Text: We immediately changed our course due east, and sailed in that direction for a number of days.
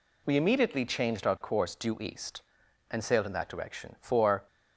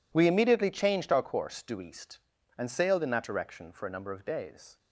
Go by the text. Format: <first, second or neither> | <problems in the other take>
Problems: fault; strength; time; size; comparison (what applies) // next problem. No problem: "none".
second | stops before "a number of days"; at 4.4 s